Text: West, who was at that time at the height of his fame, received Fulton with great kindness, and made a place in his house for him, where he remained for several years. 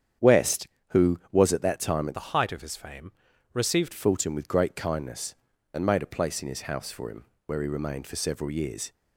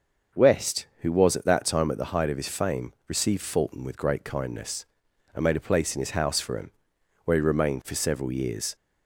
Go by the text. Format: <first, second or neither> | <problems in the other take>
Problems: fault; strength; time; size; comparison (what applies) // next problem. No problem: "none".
second | starts louder than the rest; strong; until 1.5 s; 8.5 dB; also in the second // changes voice from "the" to "received"; from 2.1 to 3.9 s; 1.8 s long